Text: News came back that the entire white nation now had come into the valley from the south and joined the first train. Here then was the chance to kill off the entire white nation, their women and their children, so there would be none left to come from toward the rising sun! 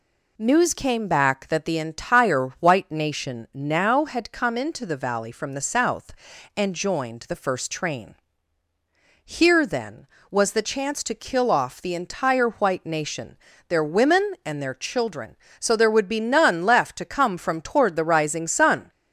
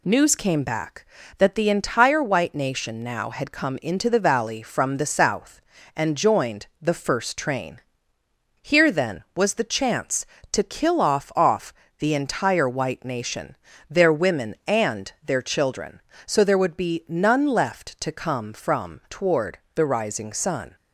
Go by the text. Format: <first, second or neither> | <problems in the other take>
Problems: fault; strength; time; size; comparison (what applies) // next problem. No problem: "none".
first | says "off" twice; at 11.3 s // pauses between "toward" and "the"; slight; at 19.5 s; 0.16 s long